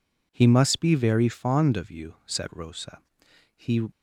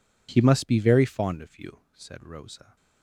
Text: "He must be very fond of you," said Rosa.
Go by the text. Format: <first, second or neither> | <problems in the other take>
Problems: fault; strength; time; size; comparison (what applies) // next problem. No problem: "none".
second | goes on to say "He"; slight; from 3.5 s on; 0.34 s long